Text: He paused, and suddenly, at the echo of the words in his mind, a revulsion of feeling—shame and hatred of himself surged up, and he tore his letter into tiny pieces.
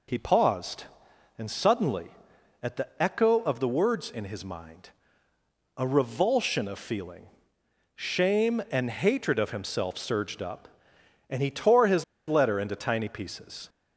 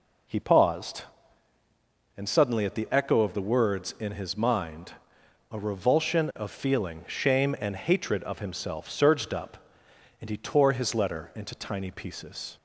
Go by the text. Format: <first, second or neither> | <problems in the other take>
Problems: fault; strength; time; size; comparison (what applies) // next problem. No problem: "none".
second | pauses between "his" and "letter"; slight; at 12.0 s; 0.26 s long